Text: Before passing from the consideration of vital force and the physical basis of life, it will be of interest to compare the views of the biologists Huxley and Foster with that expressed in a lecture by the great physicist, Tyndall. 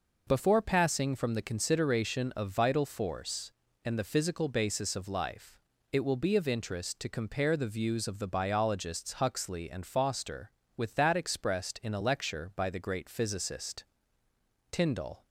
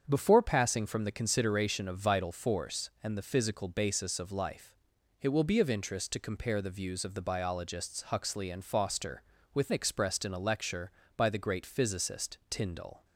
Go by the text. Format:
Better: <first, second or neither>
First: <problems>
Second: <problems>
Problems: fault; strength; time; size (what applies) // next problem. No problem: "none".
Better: first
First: none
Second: starts louder than the rest; strong; until 1.0 s; 7.5 dB // skips "that"; at 9.7 s